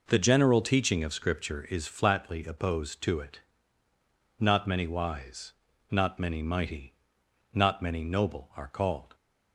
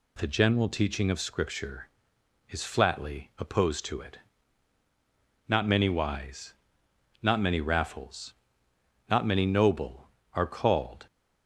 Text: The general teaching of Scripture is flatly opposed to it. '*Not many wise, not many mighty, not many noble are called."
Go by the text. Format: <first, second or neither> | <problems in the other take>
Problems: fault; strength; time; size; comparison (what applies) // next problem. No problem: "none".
first | says "raffles" for "mighty"; at 7.6 s